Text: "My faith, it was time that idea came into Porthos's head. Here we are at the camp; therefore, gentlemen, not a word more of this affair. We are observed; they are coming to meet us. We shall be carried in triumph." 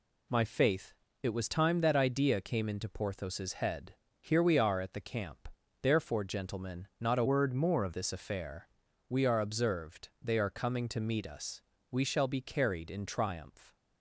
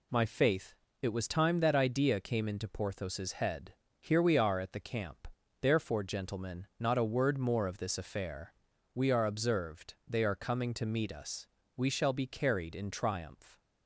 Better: second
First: changes voice from "word" to "of"; from 7.2 to 7.9 s; 0.7 s long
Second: none

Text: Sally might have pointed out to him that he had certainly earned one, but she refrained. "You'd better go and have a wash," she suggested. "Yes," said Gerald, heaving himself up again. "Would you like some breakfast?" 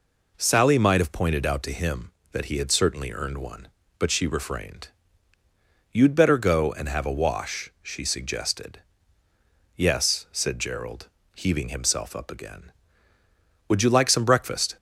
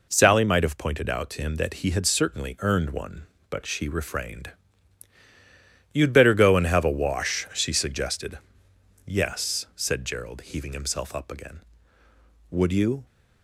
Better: first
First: none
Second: stops before "like some breakfast"; at 13.0 s

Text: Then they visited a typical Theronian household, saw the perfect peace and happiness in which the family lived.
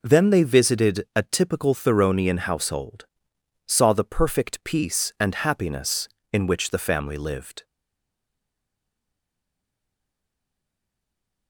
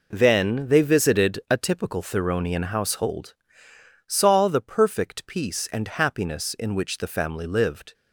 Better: second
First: stays silent after the last word; strong; from 7.6 s on; 3.8 s long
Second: none

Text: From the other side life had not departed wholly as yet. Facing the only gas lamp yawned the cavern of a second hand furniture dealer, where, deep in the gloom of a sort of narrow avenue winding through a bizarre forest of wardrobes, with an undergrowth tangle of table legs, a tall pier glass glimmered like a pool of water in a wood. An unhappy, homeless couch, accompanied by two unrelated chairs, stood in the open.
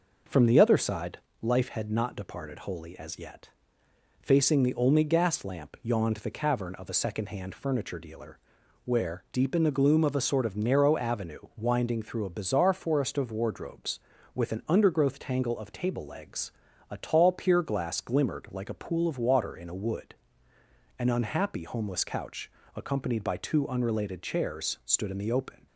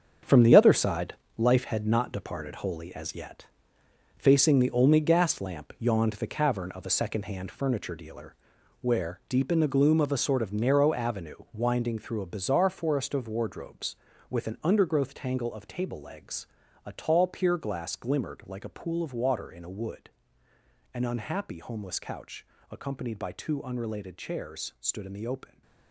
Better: first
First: pauses between "side" and "life"; slight; at 1.1 s; 0.22 s long // pauses between "avenue" and "winding"; slight; at 11.3 s; 0.18 s long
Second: gets quieter; strong; throughout; 9.5 dB // pauses between "side" and "life"; slight; at 1.1 s; 0.22 s long // pauses between "avenue" and "winding"; slight; at 11.3 s; 0.18 s long

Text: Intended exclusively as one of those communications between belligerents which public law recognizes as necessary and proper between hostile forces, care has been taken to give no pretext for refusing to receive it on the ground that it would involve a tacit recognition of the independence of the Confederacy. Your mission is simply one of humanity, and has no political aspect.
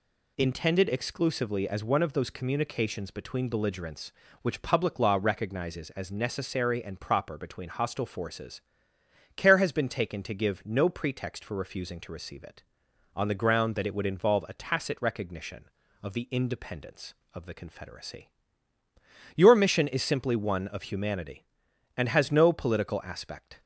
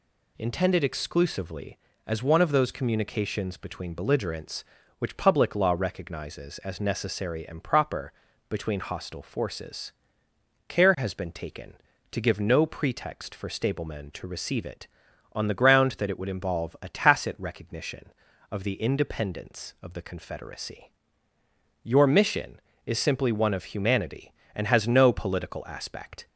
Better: first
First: none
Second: pauses between "proper" and "between"; at 8.1 s; 0.38 s long // says "stablemen" for "refusing"; at 13.4 s

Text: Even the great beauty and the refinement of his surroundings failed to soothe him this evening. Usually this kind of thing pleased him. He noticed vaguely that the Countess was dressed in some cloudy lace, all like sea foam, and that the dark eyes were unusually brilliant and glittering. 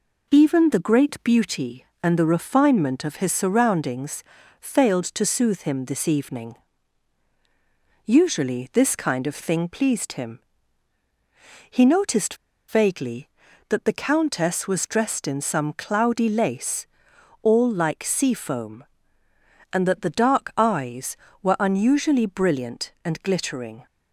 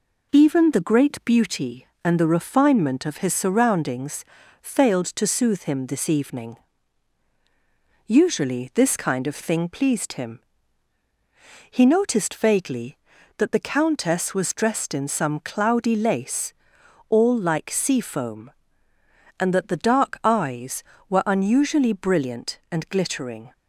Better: second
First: pauses between "surroundings" and "failed"; at 4.2 s; 0.38 s long // pauses between "noticed" and "vaguely"; slight; at 12.3 s; 0.34 s long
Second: pauses between "surroundings" and "failed"; at 4.2 s; 0.38 s long

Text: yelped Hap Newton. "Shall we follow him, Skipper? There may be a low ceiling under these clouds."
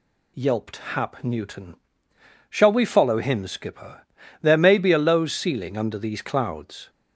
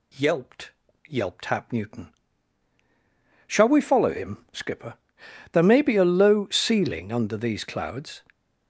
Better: first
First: none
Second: says "yelped" twice; at 1.0 s

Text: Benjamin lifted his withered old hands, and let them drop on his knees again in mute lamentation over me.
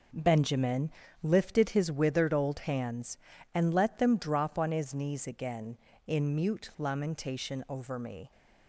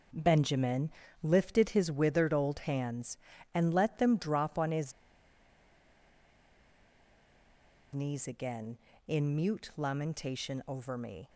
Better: first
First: pauses between "Benjamin" and "lifted"; slight; at 0.8 s; 0.32 s long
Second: pauses between "Benjamin" and "lifted"; slight; at 0.8 s; 0.32 s long // pauses between "his" and "knees"; strong; at 4.9 s; 3.0 s long

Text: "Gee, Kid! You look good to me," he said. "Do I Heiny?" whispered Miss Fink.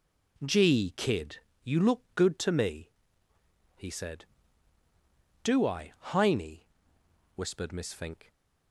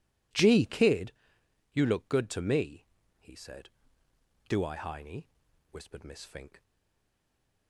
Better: first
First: none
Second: stays silent after the last word; from 6.6 s on; 1.0 s long

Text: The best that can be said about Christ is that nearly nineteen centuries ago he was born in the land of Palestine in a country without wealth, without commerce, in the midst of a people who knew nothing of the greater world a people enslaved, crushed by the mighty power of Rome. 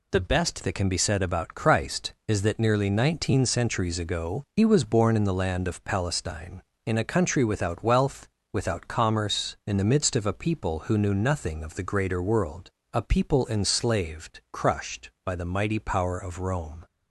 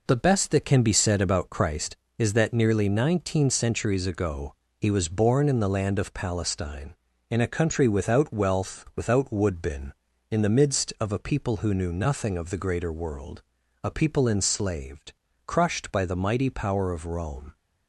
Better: first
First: pauses between "world" and "a"; slight; at 12.7 s; 0.20 s long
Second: pauses between "ago" and "he"; slight; at 4.5 s; 0.26 s long // says "woodbin" for "commerce"; at 9.3 s // pauses between "world" and "a"; at 13.4 s; 0.40 s long

